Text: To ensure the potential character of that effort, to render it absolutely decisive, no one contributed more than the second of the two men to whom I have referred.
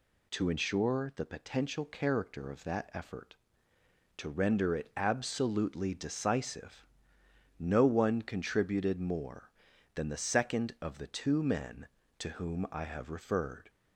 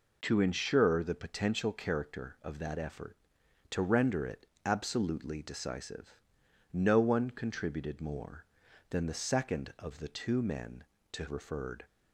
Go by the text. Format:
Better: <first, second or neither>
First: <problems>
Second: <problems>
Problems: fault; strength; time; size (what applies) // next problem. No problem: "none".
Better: first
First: none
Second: pauses between "it" and "absolutely"; slight; at 4.4 s; 0.18 s long // skips "whom I have"; at 11.2 s